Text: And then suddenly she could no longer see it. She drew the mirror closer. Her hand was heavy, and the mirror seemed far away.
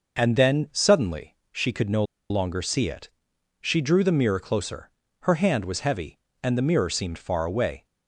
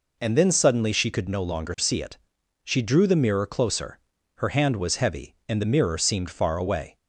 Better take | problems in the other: second | pauses between "suddenly" and "she"; slight; at 1.3 s; 0.16 s long // pauses between "no" and "longer"; slight; at 2.0 s; 0.26 s long

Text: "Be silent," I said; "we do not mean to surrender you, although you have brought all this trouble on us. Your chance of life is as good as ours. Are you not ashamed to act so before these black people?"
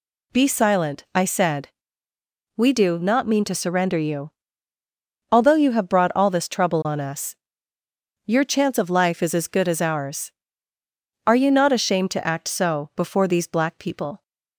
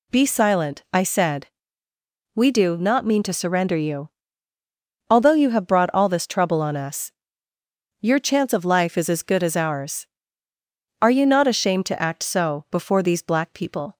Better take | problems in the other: neither | none

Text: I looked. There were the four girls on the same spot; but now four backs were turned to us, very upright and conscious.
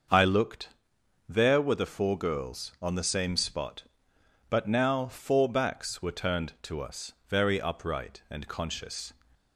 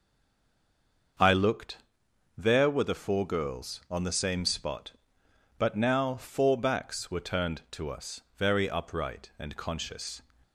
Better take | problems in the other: first | stays silent before the first word; until 1.1 s; 1.1 s long // starts louder than the rest; until 2.7 s; 6.5 dB; also in the first

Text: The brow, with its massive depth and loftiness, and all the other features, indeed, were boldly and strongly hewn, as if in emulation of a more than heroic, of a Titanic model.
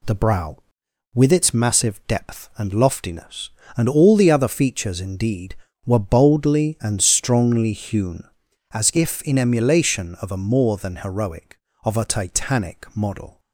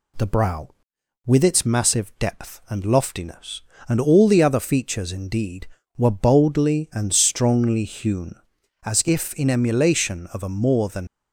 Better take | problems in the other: first | stops before "heroic of a Titanic model"; at 11.0 s

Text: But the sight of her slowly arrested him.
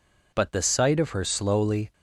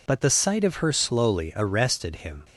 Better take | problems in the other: second | stops before "arrested him"; at 1.9 s

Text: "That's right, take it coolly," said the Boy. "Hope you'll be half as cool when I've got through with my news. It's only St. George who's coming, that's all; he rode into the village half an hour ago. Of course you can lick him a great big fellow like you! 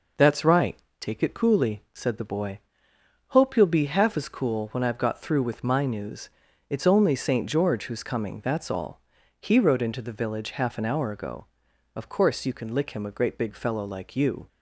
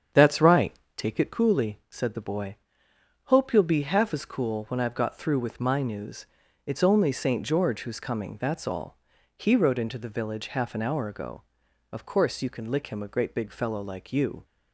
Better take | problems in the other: first | starts louder than the rest; strong; until 1.3 s; 8 dB

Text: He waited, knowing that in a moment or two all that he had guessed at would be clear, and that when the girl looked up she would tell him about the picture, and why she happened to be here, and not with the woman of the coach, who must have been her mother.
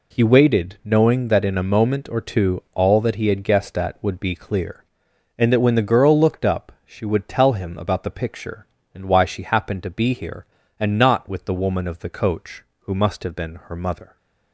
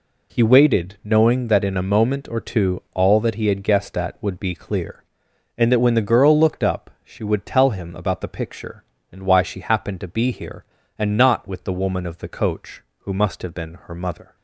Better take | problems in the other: neither | none

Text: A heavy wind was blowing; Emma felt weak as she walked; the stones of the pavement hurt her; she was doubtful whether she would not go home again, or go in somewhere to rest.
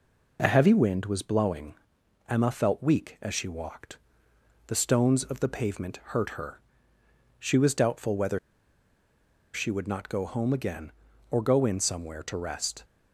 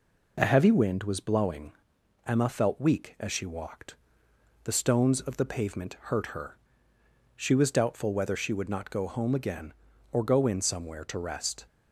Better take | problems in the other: second | pauses between "pavement" and "hurt"; slight; at 5.9 s; 0.18 s long; slight in the second // pauses between "whether" and "she"; at 8.3 s; 1.1 s long

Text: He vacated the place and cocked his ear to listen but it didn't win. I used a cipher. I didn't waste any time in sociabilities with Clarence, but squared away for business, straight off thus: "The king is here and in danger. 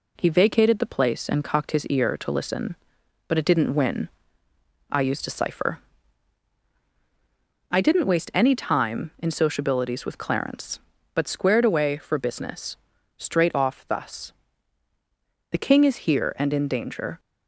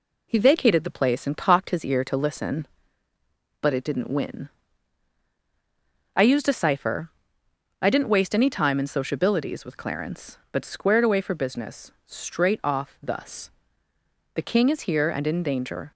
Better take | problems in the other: neither | none

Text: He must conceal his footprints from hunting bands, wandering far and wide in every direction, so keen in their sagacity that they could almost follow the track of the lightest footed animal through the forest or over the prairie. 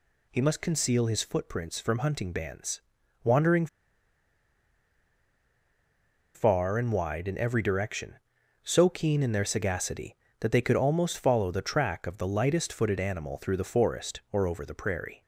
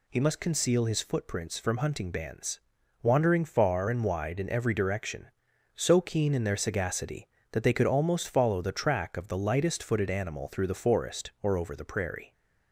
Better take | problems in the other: second | pauses between "wandering" and "far"; strong; at 3.6 s; 2.6 s long

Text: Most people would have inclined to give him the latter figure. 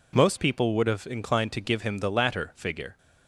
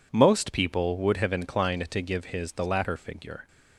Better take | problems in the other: first | says "his" for "him"; at 2.2 s

